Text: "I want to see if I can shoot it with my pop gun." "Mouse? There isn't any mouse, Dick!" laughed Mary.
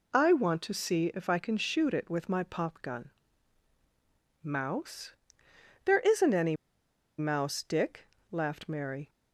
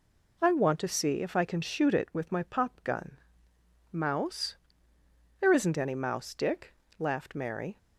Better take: second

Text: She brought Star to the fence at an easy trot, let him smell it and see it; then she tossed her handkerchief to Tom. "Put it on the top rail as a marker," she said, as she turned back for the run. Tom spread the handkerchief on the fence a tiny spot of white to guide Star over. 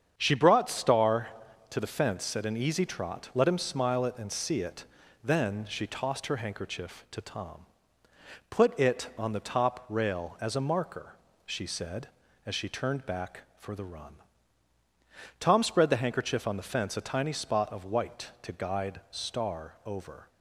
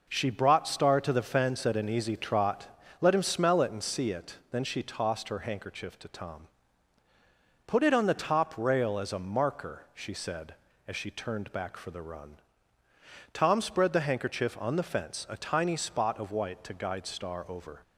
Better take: second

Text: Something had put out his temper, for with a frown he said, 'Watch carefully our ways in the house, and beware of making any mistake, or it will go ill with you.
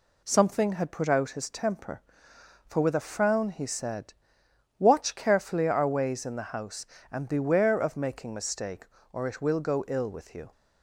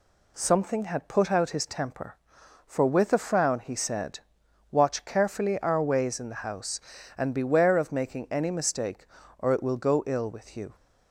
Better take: second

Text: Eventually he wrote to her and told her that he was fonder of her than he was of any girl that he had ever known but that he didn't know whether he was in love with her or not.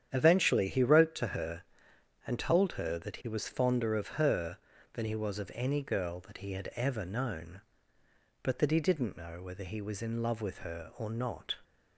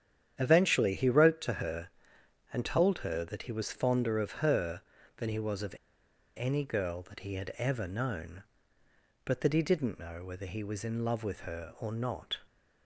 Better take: first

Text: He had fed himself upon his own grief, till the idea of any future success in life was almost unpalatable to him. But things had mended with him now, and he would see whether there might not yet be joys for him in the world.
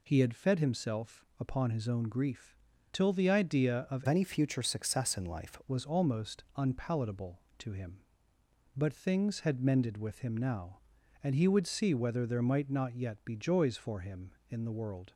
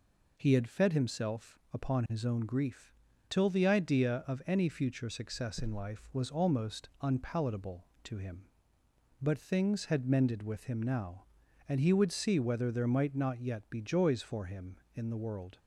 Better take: second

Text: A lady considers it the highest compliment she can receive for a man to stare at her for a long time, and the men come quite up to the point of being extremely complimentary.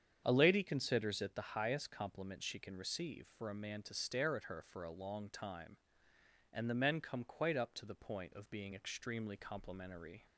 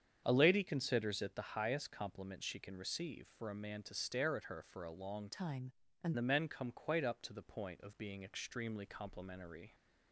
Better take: first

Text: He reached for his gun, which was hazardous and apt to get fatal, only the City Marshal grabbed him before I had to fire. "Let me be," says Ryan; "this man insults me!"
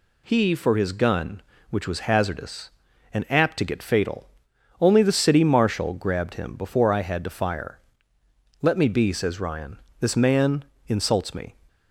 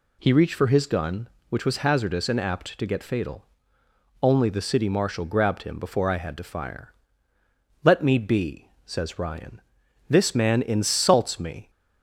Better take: second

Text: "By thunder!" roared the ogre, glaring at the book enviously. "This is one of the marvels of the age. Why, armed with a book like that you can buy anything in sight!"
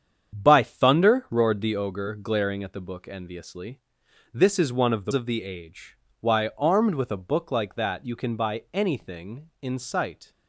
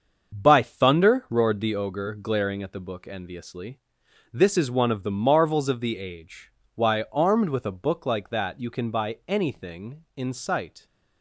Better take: second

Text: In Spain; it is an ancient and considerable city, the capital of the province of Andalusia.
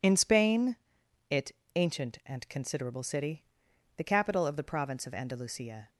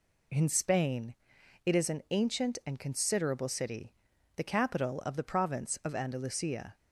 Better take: second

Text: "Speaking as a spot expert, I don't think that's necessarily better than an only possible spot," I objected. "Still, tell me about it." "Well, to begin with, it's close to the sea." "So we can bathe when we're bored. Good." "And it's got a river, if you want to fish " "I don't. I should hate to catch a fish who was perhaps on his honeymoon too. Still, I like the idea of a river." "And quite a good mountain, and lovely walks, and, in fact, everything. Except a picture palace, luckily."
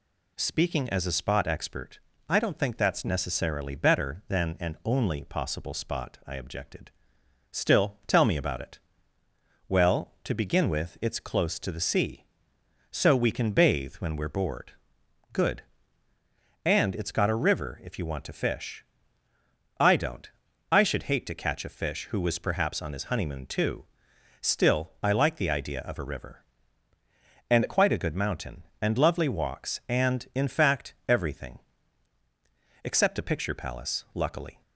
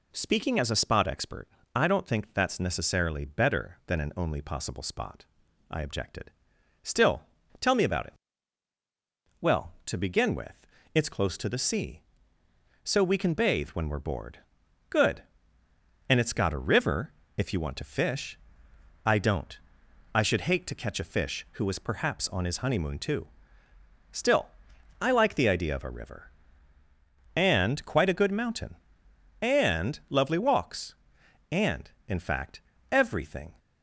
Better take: first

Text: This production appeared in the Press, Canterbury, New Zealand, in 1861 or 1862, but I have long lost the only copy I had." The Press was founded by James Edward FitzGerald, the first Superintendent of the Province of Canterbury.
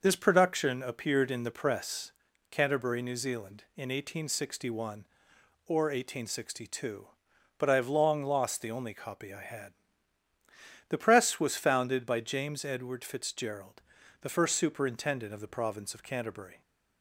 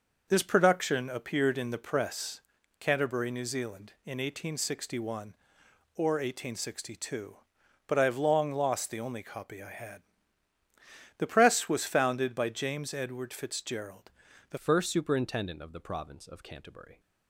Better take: first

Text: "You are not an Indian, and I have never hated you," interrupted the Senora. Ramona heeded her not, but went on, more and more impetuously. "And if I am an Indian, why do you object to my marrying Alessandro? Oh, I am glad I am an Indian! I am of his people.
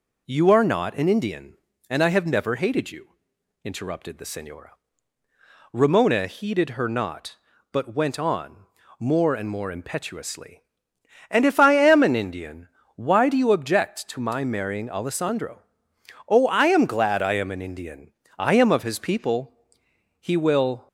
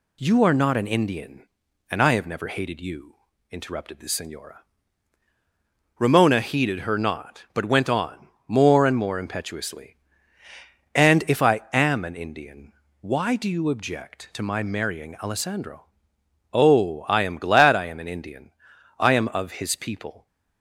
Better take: second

